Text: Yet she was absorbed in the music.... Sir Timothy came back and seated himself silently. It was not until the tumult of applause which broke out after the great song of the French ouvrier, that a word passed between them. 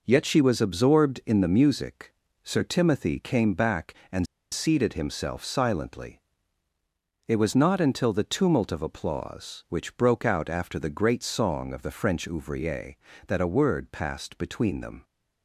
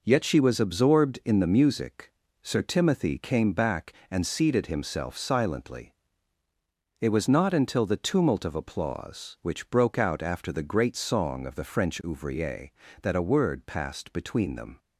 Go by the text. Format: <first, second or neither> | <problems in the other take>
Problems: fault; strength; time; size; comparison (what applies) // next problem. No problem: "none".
second | pauses between "and" and "seated"; slight; at 4.2 s; 0.27 s long